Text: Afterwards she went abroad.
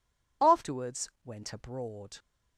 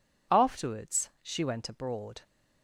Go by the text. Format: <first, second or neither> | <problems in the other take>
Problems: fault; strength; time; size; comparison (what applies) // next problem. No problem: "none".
second | skips "she"; at 1.1 s